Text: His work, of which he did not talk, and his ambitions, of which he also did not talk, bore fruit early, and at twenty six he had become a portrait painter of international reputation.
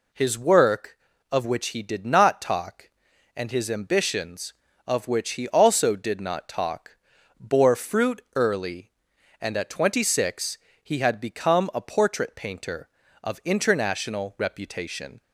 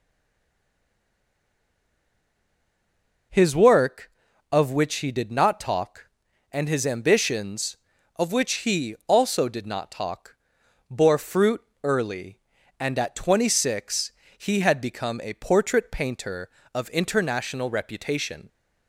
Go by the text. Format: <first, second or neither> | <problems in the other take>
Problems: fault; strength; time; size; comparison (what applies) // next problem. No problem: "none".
first | stays silent before the first word; strong; until 3.2 s; 3.2 s long // pauses between "fruit" and "early"; slight; at 11.6 s; 0.22 s long // pauses between "six" and "he"; slight; at 14.1 s; 0.26 s long; slight in the first